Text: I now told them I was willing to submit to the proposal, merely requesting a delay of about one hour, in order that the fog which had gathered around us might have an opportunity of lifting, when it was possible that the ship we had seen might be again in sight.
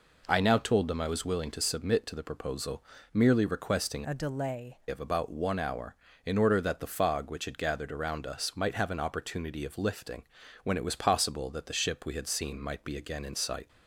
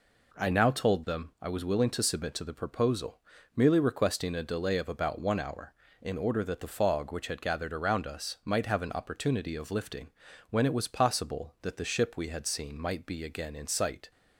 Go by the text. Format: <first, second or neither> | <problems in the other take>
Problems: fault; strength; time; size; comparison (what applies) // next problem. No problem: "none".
second | changes voice from "a" to "delay"; from 4.0 to 4.7 s; 0.7 s long